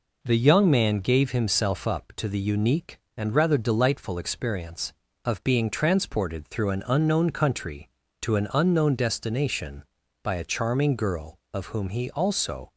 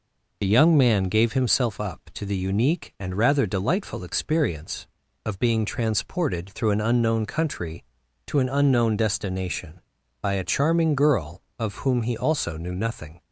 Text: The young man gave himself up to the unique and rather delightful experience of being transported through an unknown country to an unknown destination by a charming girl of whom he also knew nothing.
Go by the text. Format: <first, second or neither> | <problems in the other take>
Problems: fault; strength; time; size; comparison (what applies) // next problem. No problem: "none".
second | stops before "knew nothing"; at 12.7 s